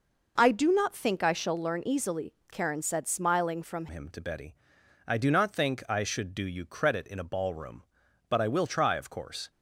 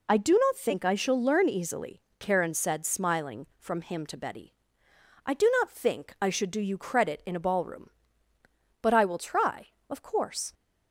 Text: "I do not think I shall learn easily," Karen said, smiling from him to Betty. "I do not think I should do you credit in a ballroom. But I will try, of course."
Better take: second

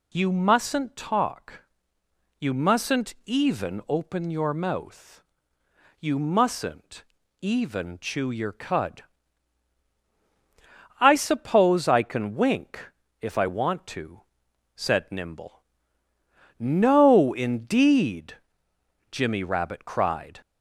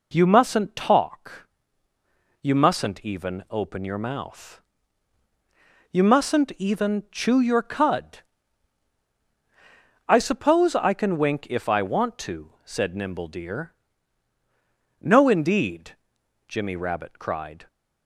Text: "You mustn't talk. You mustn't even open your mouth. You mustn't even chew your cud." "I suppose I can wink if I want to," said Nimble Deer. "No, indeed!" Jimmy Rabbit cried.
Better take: second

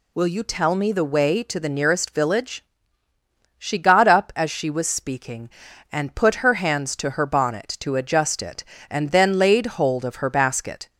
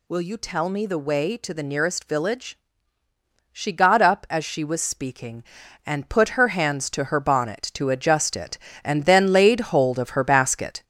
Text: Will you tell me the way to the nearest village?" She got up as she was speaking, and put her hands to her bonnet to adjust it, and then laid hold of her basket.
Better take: first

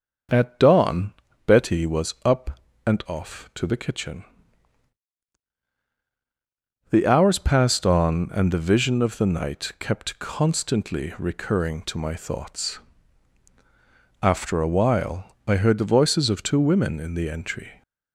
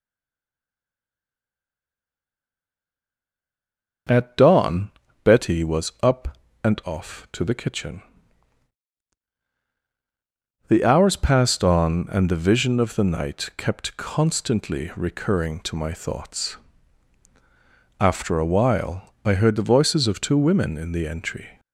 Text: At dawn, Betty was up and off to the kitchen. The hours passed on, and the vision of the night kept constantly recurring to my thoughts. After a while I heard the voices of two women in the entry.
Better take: first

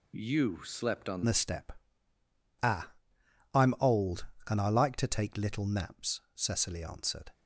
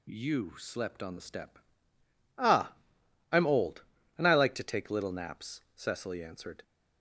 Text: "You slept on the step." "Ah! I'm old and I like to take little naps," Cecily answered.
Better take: second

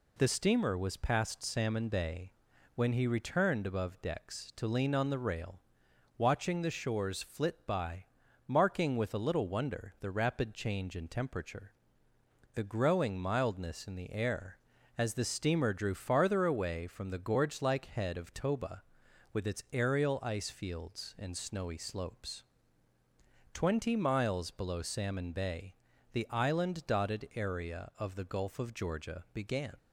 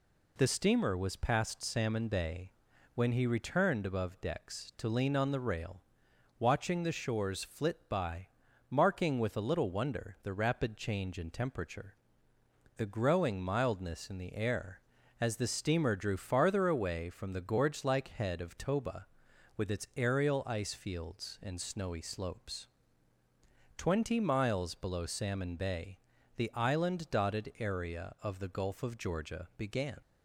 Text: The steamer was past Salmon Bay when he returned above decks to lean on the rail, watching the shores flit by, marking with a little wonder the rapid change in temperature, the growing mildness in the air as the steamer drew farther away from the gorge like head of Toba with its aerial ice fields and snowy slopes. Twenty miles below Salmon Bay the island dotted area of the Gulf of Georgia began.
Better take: neither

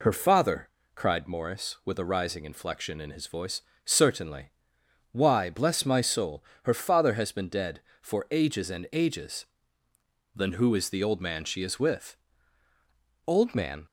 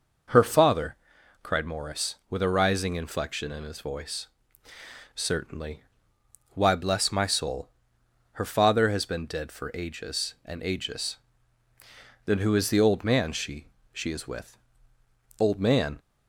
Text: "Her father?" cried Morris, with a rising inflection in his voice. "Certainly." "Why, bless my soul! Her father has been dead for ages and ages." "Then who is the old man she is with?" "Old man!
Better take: first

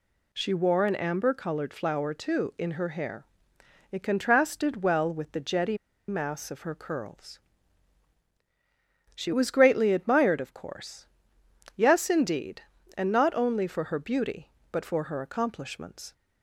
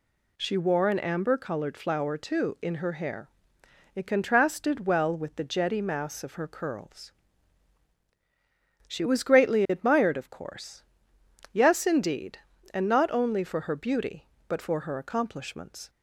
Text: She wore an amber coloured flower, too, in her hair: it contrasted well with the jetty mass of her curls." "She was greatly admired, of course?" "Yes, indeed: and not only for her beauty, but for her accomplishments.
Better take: second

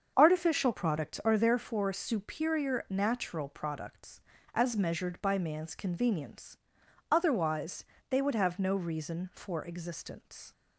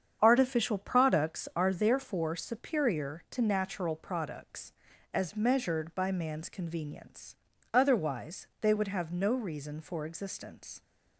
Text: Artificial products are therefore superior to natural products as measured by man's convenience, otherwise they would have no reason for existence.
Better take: second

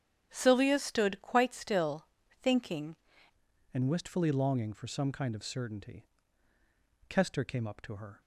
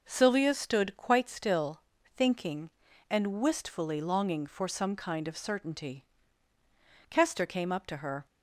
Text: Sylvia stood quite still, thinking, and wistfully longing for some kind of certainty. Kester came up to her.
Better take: second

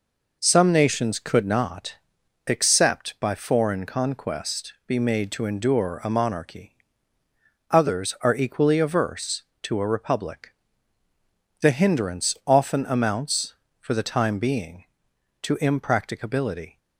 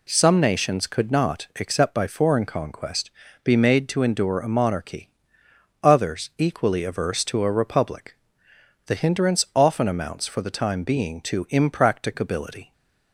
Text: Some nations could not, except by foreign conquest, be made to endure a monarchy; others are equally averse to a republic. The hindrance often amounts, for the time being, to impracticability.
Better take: first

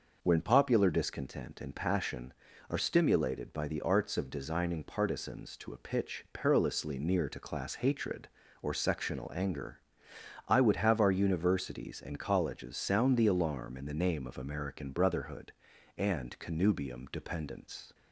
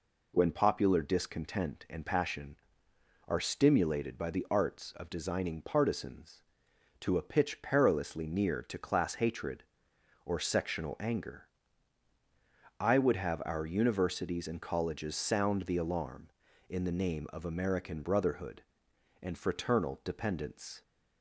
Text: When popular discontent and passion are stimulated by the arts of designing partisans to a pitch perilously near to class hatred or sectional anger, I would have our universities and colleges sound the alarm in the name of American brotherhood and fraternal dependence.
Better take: second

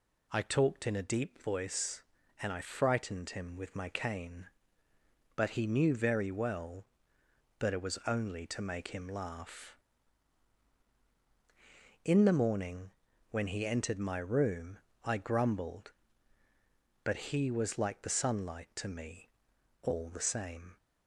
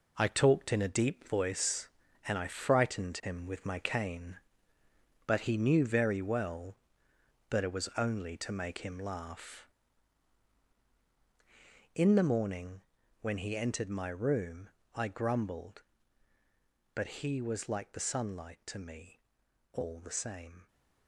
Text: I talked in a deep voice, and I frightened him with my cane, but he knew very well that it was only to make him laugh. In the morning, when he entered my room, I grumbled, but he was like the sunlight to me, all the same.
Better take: first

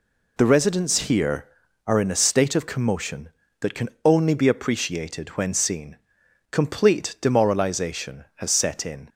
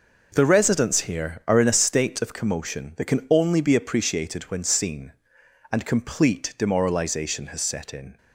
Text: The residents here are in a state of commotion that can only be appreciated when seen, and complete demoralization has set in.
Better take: second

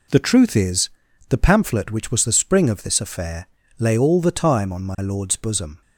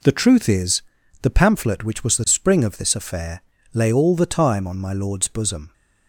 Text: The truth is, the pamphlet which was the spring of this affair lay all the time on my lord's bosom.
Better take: neither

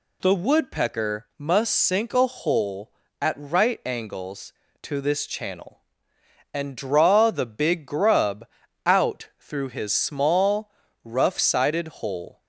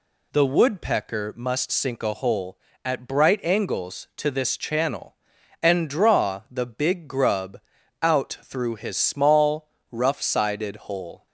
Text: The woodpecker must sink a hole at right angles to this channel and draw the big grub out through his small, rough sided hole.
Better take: first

